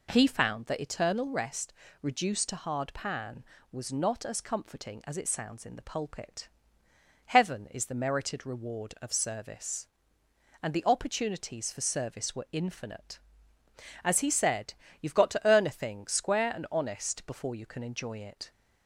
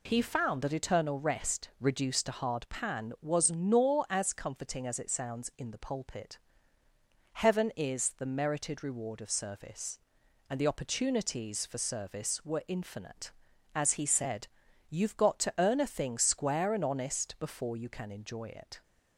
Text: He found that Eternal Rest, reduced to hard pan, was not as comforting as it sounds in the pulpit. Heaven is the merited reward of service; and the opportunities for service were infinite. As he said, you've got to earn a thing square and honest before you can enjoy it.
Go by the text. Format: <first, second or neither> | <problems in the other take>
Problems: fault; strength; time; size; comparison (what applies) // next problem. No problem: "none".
first | says "nor" for "not"; at 3.5 s